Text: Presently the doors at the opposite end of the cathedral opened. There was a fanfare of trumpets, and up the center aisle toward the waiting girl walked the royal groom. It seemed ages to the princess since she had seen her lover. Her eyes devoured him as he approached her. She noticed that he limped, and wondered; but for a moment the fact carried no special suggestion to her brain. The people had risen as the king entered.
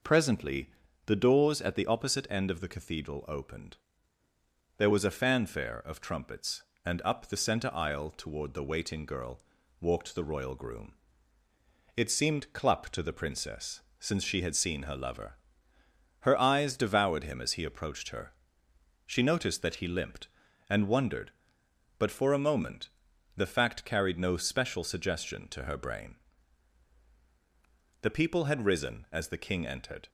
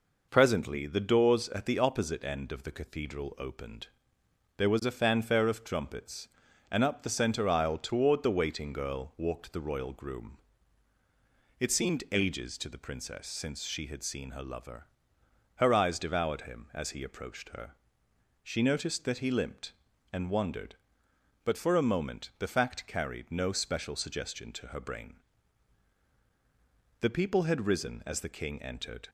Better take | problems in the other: second | pauses between "Presently" and "the"; slight; at 0.6 s; 0.36 s long // pauses between "girl" and "walked"; at 9.4 s; 0.40 s long // says "clup" for "ages"; at 12.5 s // pauses between "princess" and "since"; slight; at 13.8 s; 0.20 s long // pauses between "moment" and "the"; noticeable; at 22.8 s; 0.48 s long

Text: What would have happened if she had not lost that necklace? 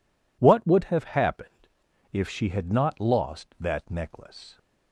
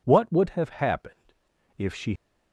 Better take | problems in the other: first | pauses between "happened" and "if"; at 1.3 s; 0.44 s long; also in the first // stops before "had not lost that necklace"; at 2.1 s

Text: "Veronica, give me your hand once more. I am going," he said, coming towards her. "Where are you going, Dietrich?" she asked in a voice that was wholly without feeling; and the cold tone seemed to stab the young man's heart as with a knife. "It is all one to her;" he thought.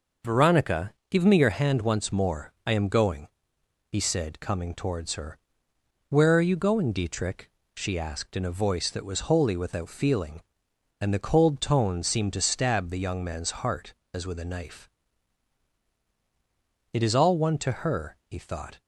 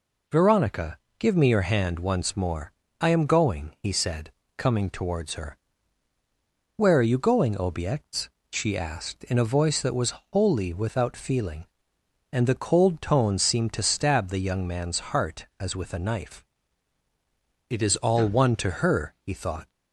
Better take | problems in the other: first | says "Obiects" for "Dietrich"; at 7.5 s // pauses between "was" and "wholly"; slight; at 10.1 s; 0.18 s long

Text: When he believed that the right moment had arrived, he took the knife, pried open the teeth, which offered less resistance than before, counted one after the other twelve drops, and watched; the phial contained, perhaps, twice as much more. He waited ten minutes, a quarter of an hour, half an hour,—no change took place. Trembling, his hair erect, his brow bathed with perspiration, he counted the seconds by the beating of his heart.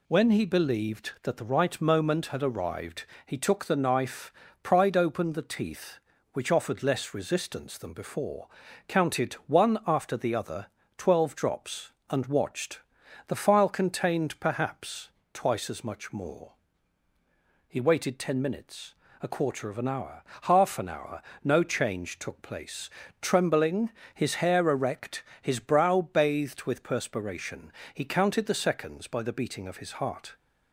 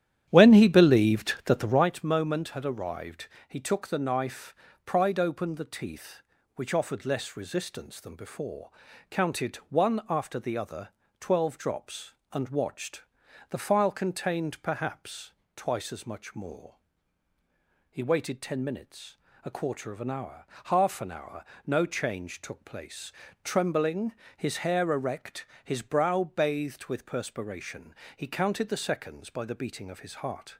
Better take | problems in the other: first | starts louder than the rest; strong; until 1.9 s; 11 dB // pauses between "other" and "twelve"; slight; at 10.8 s; 0.32 s long; slight in the first

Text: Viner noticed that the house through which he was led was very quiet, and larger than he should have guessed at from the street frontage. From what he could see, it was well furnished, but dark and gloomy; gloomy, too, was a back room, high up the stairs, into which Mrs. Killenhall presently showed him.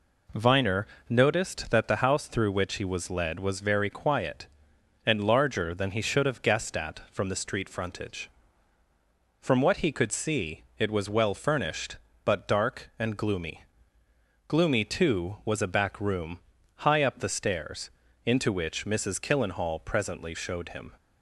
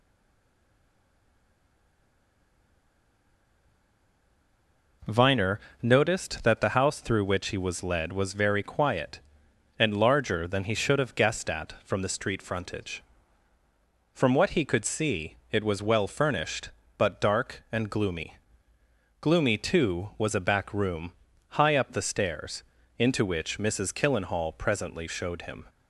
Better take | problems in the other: first | stays silent before the first word; strong; until 5.0 s; 5.0 s long // pauses between "Viner" and "noticed"; slight; at 5.5 s; 0.22 s long; slight in the first

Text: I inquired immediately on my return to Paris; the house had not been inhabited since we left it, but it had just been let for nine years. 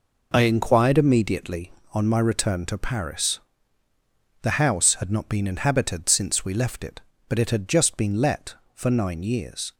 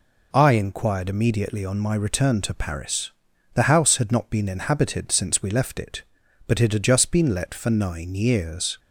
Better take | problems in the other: neither | none

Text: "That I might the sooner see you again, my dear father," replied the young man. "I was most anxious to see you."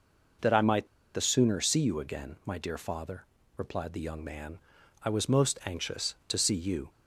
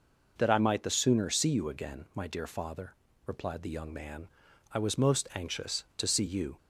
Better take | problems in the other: second | pauses between "might" and "the"; slight; at 0.8 s; 0.27 s long

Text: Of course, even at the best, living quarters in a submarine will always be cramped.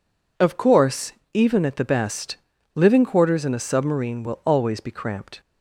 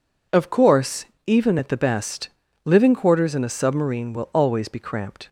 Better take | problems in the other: neither | none

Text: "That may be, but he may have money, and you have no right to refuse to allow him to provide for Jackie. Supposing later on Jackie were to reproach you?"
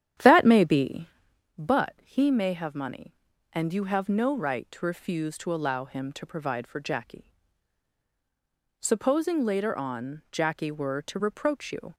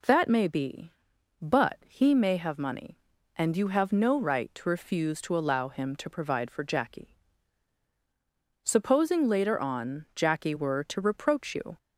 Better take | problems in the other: second | starts louder than the rest; strong; until 1.6 s; 10 dB

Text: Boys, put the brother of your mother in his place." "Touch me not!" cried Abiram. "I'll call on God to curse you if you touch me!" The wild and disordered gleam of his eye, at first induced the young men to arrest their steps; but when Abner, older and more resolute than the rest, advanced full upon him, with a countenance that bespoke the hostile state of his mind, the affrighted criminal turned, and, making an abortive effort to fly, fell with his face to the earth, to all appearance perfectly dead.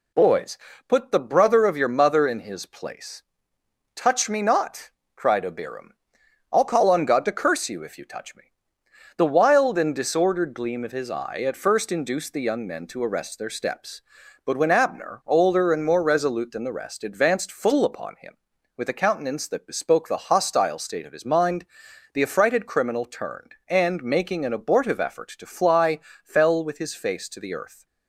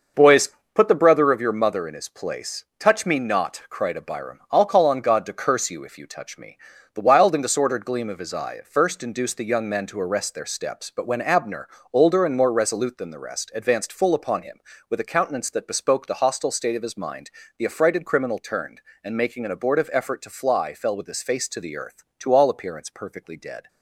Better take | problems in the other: second | stops before "to all appearance perfectly dead"; at 27.8 s

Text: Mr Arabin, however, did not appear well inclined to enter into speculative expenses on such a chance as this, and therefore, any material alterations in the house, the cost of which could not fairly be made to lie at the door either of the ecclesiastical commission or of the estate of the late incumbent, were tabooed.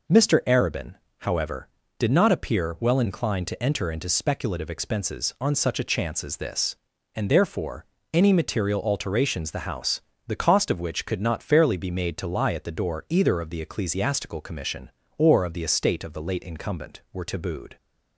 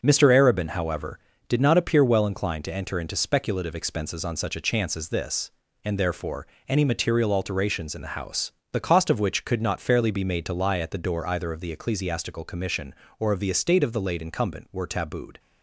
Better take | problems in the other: second | skips "in"; at 9.5 s

